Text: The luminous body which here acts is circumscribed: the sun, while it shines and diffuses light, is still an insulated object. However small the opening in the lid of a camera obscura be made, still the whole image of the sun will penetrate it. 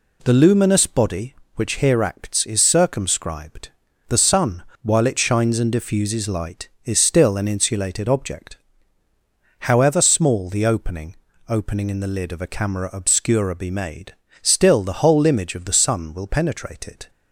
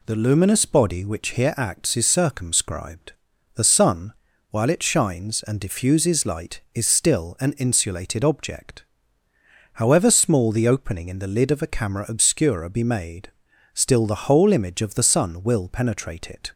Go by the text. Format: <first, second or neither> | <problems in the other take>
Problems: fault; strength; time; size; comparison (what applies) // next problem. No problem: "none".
second | says "opening" twice; at 11.4 s